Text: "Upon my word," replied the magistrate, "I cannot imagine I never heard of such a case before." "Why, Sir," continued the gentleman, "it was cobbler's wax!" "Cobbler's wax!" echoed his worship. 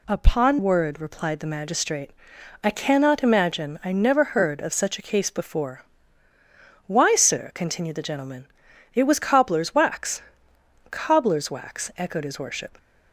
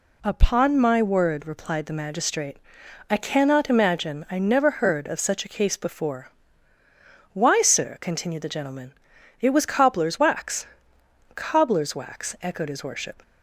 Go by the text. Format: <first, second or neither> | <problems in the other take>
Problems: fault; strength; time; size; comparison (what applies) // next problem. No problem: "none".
second | skips "my"; at 0.5 s